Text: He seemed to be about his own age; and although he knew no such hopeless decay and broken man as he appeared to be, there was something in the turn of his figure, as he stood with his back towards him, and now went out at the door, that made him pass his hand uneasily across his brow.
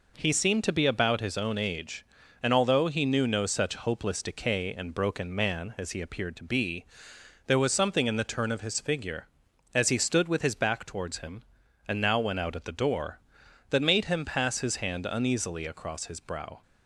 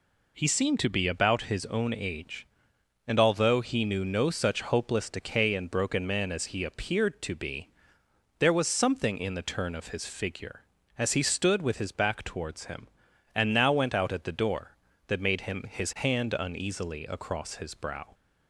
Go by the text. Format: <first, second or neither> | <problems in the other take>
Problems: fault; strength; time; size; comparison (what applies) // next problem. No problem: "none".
first | skips "pass"; at 15.6 s